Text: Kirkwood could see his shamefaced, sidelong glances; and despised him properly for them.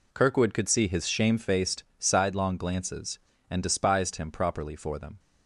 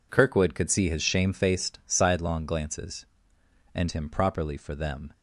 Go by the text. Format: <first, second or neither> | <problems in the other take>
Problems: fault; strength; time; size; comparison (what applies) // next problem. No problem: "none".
first | skips "despised"; at 3.8 s